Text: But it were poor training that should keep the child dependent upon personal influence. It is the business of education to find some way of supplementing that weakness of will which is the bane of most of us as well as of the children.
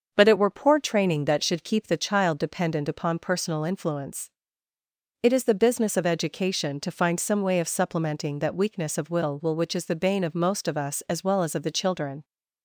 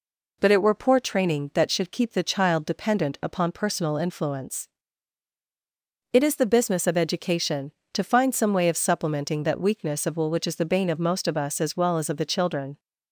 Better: second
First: starts louder than the rest; until 1.1 s; 6.5 dB // says "will" twice; at 9.4 s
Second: none

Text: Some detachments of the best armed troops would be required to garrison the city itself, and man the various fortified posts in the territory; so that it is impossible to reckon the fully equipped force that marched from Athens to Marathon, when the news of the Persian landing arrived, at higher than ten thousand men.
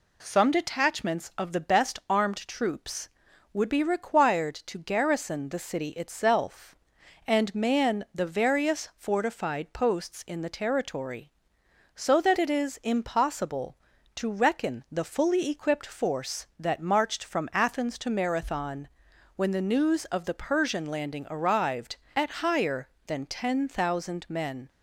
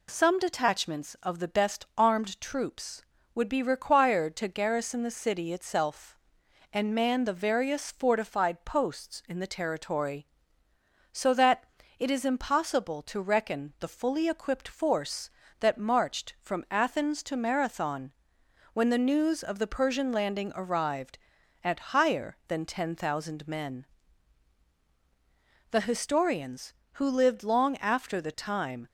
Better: first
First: none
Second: pauses between "that" and "it"; slight; at 11.6 s; 0.36 s long // goes on to say "The historians who lived long after the time"; strong; from 25.6 s on; 3.1 s long

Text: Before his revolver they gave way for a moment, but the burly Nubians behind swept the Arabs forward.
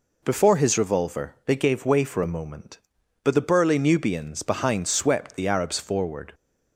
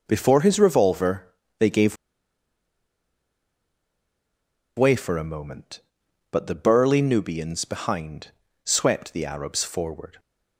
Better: first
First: none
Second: pauses between "revolver" and "they"; slight; at 1.2 s; 0.32 s long // pauses between "gave" and "way"; strong; at 1.9 s; 2.8 s long // pauses between "behind" and "swept"; slight; at 8.3 s; 0.32 s long

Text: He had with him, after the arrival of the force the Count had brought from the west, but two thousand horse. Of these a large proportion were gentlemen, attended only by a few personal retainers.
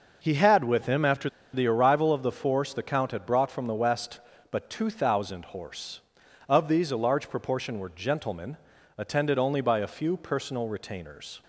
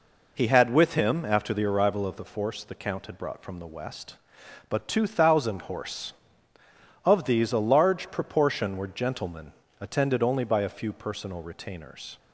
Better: second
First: pauses between "after" and "the"; slight; at 1.2 s; 0.25 s long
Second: none

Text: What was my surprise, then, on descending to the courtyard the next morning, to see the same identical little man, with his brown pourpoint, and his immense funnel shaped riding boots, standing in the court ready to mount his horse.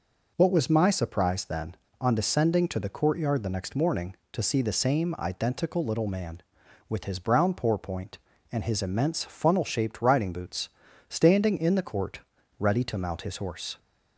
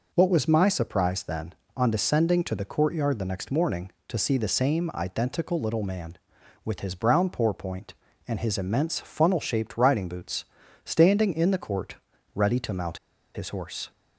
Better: first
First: pauses between "court" and "ready"; at 12.2 s; 0.38 s long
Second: pauses between "court" and "ready"; at 11.9 s; 0.38 s long // pauses between "mount" and "his"; at 12.9 s; 0.36 s long

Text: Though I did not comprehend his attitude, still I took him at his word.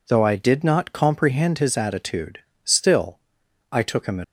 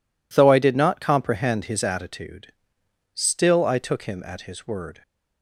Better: second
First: pauses between "still" and "I"; noticeable; at 3.1 s; 0.52 s long // stops before "his word"; at 4.2 s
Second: none

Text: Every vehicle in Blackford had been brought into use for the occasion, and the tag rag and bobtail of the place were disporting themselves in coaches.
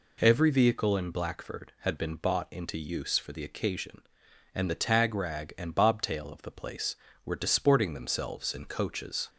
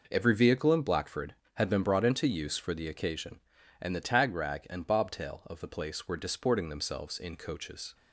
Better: second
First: says "bought" for "brought"; at 2.1 s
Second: none

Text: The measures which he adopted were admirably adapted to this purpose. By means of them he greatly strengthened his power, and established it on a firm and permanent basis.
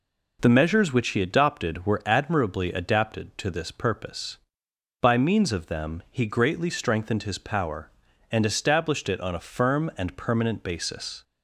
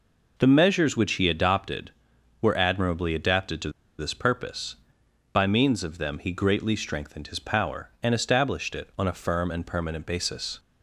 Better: first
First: none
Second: pauses between "to" and "this"; slight; at 3.7 s; 0.28 s long

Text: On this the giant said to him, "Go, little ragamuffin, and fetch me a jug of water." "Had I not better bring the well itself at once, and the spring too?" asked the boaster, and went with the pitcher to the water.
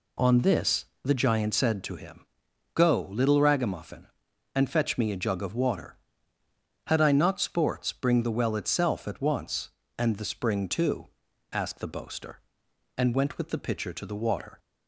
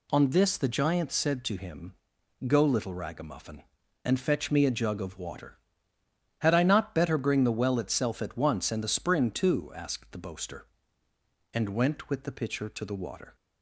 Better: second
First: pauses between "this" and "the"; slight; at 0.8 s; 0.18 s long // says "sports" for "better"; at 7.3 s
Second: none

